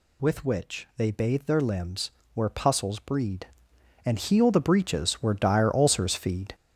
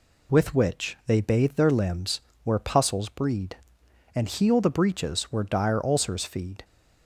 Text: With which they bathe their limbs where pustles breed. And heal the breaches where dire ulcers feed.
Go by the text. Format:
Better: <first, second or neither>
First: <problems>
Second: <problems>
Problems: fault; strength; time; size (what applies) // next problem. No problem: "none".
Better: second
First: gets louder; strong; throughout; 7.5 dB // pauses between "limbs" and "where"; slight; at 2.1 s; 0.24 s long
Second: pauses between "limbs" and "where"; slight; at 2.2 s; 0.24 s long